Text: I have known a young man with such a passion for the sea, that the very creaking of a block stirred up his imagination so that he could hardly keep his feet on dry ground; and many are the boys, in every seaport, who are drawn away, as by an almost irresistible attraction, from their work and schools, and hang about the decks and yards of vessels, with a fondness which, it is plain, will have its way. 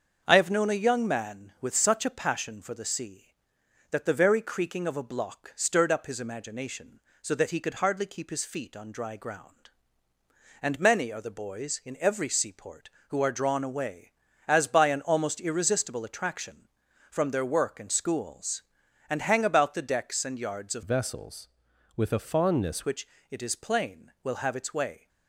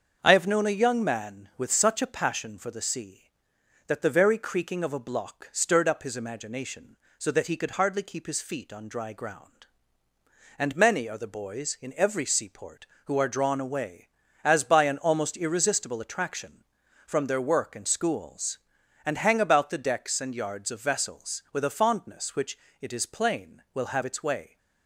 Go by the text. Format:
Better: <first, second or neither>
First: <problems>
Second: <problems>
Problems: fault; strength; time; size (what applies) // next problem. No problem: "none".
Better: second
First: starts louder than the rest; until 1.2 s; 6.5 dB // changes voice from "vessels" to "fondness"; from 20.8 to 22.8 s; 2.0 s long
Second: starts louder than the rest; until 1.2 s; 6.5 dB